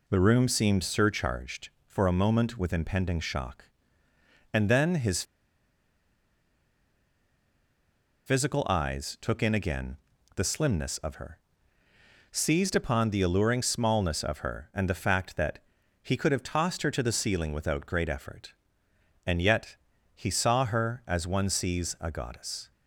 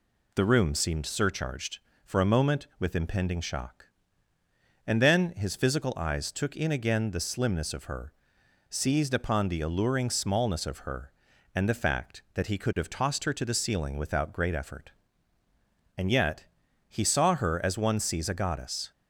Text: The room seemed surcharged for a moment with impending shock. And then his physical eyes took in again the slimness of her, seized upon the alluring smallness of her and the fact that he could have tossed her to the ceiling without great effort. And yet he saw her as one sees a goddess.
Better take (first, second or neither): second